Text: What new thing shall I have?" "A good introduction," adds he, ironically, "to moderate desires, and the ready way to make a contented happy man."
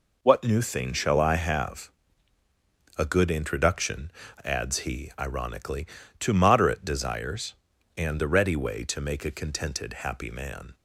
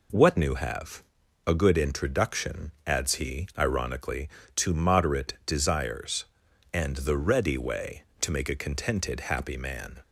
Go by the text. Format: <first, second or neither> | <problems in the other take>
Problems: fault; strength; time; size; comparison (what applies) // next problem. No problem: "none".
first | skips "thing shall I"; at 0.5 s